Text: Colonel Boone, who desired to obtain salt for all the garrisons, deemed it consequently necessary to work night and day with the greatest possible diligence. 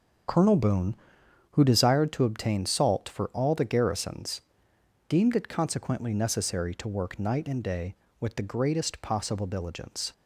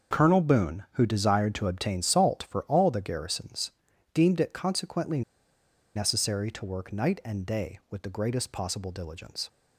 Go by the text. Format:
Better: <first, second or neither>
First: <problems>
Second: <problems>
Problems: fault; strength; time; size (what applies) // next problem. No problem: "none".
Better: first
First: starts louder than the rest; strong; until 1.8 s; 7 dB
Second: starts louder than the rest; noticeable; until 1.2 s; 6 dB // pauses between "consequently" and "necessary"; noticeable; at 5.2 s; 0.73 s long